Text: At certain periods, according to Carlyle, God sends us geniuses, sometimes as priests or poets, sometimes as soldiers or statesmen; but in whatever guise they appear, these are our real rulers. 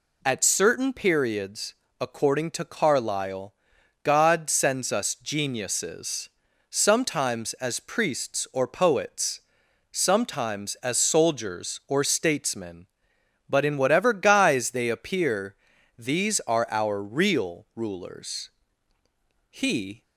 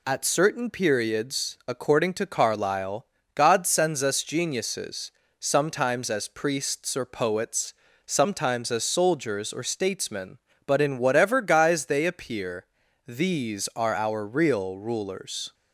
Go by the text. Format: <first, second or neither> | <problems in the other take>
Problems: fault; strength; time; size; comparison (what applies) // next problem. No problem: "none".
second | goes on to say "He"; from 19.4 s on; 0.54 s long